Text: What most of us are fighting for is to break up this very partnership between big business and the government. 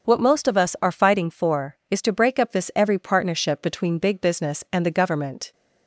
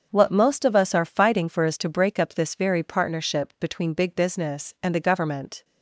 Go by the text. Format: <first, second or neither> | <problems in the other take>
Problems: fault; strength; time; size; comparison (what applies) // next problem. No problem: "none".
second | starts louder than the rest; until 1.1 s; 6.5 dB; also in the second // says "every" for "very"; at 2.7 s